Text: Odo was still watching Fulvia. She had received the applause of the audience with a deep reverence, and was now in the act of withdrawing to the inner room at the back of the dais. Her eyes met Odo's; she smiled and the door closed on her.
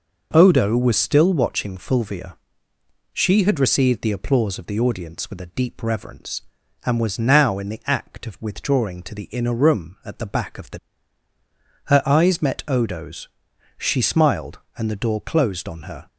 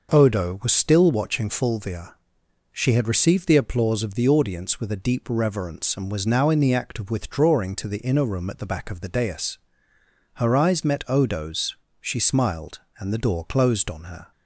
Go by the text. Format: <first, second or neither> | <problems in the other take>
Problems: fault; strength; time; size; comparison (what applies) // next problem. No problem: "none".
second | skips "dais"; at 11.3 s